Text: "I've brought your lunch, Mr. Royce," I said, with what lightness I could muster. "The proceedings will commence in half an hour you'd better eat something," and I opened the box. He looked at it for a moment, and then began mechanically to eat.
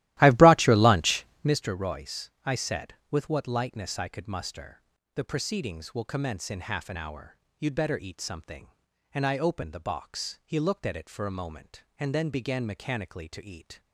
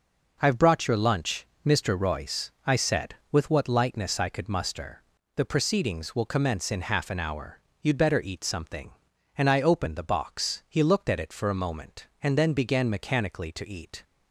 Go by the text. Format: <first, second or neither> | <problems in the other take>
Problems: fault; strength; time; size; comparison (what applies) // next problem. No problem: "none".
second | starts louder than the rest; strong; until 1.6 s; 15.5 dB // pauses between "hour" and "you'd"; slight; at 7.3 s; 0.24 s long; slight in the second